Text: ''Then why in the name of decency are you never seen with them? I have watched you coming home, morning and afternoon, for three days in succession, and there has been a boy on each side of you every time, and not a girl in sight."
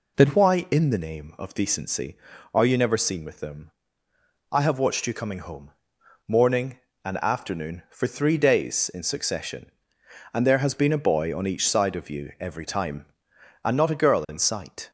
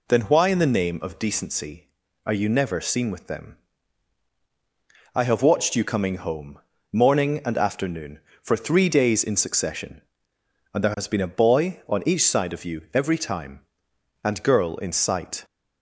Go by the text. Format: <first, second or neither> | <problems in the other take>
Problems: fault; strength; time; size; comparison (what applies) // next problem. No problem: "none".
first | skips "not a"; at 14.4 s